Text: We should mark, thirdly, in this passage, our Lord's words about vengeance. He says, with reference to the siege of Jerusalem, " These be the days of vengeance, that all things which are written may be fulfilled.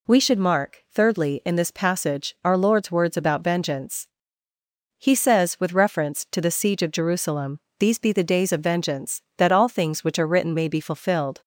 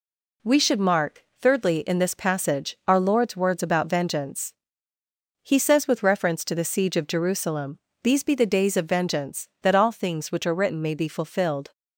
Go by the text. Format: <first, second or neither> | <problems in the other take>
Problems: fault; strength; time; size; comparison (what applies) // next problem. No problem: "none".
first | gets quieter; noticeable; throughout; 4.5 dB